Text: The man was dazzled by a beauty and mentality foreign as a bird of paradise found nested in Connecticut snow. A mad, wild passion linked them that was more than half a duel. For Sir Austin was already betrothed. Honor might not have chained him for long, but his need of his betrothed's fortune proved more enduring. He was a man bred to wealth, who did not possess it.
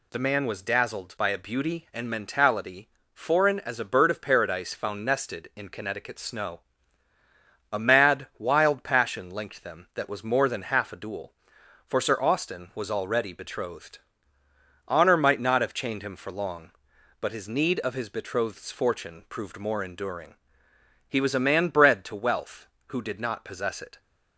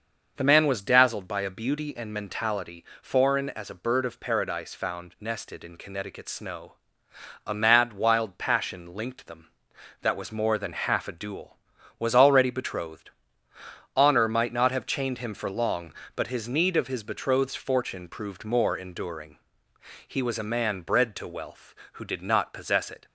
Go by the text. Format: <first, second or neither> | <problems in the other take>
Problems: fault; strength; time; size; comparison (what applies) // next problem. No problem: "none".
first | starts louder than the rest; noticeable; until 1.3 s; 6 dB // pauses between "mentality" and "foreign"; slight; at 2.8 s; 0.18 s long; slight in the first // skips "For Sir Austin"; at 11.7 s